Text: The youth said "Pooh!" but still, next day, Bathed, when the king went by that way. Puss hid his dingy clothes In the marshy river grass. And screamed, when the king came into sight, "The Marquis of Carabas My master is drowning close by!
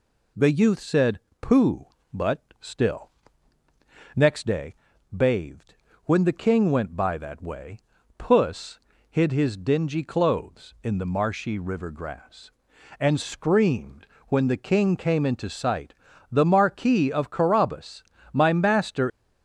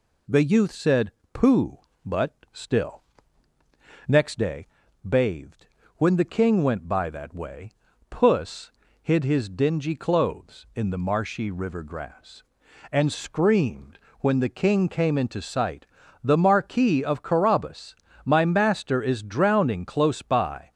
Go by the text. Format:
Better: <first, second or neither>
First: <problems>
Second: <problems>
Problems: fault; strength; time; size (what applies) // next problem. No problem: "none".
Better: second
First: pauses between "said" and "Pooh"; slight; at 1.1 s; 0.22 s long // pauses between "but" and "still"; slight; at 2.4 s; 0.18 s long // pauses between "Puss" and "hid"; slight; at 8.7 s; 0.30 s long // pauses between "Carabas" and "My"; slight; at 18.0 s; 0.30 s long // stops before "is drowning close by"; at 19.1 s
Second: pauses between "said" and "Pooh"; slight; at 1.1 s; 0.22 s long // pauses between "but" and "still"; slight; at 2.3 s; 0.18 s long // pauses between "Puss" and "hid"; slight; at 8.7 s; 0.30 s long // pauses between "Carabas" and "My"; slight; at 17.9 s; 0.30 s long